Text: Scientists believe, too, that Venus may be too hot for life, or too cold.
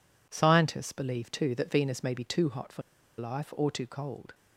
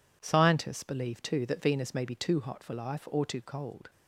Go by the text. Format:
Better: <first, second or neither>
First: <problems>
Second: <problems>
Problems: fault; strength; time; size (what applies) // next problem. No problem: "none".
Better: second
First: pauses between "for" and "life"; at 2.8 s; 0.36 s long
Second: none